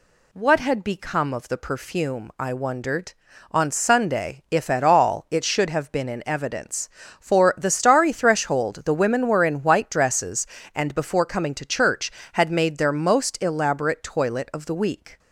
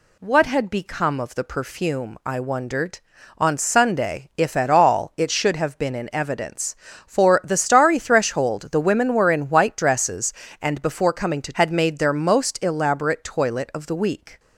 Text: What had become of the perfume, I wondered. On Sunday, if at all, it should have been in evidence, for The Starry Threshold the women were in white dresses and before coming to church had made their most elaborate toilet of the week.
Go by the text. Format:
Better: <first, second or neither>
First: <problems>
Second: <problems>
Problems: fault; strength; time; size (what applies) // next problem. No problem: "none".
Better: first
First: none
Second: skips "church"; at 11.5 s